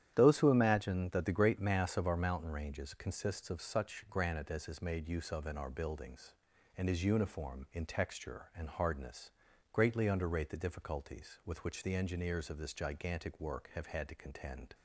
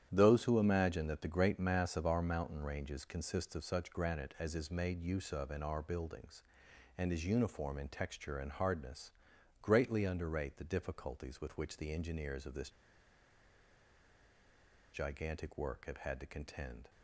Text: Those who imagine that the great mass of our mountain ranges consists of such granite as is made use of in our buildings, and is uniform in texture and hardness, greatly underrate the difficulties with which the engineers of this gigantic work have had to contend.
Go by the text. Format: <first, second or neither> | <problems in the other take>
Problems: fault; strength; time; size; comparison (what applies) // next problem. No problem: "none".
first | starts louder than the rest; strong; until 1.1 s; 10 dB; strong in the first // pauses between "this" and "gigantic"; strong; at 12.6 s; 2.2 s long